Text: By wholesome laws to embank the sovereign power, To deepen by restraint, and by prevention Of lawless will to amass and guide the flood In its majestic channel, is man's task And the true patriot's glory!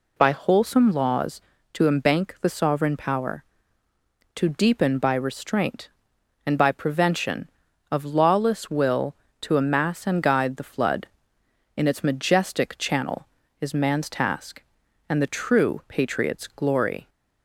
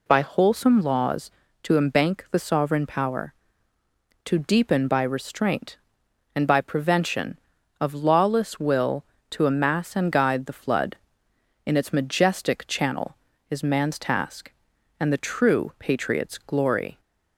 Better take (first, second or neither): neither